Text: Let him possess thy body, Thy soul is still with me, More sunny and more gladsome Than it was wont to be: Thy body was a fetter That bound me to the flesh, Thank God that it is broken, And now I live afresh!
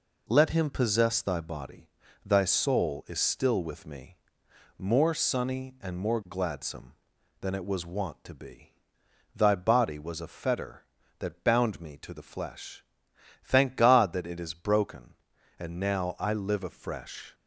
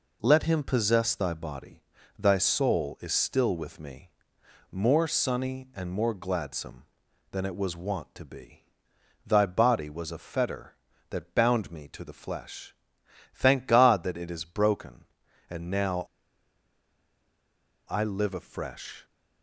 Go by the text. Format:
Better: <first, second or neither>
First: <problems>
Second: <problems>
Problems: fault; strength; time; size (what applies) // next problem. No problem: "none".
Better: first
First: none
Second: pauses between "now" and "I"; strong; at 16.0 s; 1.8 s long